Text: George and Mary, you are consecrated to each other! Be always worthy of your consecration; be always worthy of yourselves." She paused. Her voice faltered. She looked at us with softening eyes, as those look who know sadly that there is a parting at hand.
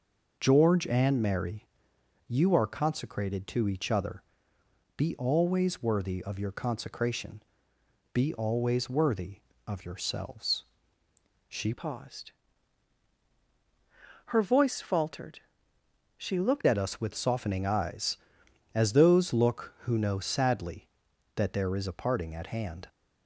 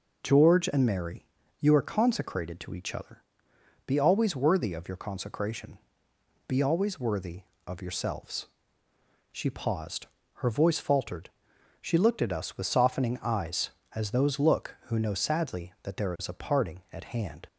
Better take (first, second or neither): second